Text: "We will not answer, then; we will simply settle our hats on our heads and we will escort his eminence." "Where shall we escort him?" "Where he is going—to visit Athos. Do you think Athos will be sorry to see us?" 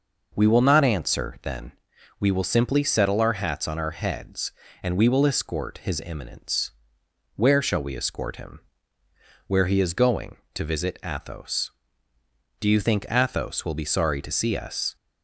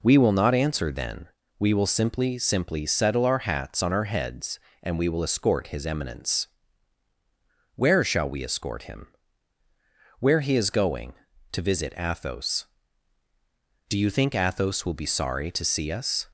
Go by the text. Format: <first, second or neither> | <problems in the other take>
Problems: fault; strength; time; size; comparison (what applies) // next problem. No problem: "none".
first | says "simply" twice; at 2.3 s